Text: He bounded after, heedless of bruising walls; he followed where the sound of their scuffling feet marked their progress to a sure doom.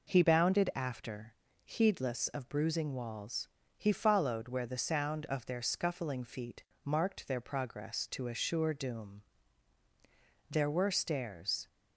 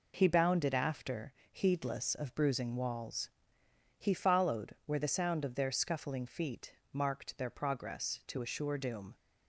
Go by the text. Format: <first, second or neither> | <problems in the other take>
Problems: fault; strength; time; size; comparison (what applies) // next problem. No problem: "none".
second | pauses between "feet" and "marked"; slight; at 6.6 s; 0.22 s long; slight in the second // goes on to say "There were stairs"; noticeable; from 10.5 s on; 1.1 s long